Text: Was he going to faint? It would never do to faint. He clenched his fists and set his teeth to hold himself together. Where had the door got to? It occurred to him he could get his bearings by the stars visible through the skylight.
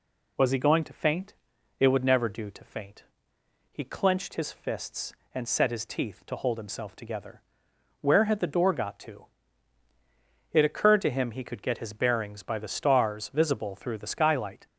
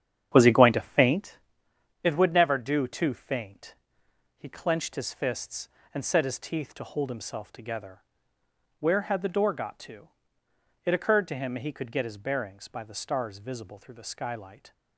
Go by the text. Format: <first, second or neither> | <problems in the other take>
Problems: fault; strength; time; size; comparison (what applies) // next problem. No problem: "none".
first | starts louder than the rest; strong; until 1.2 s; 9 dB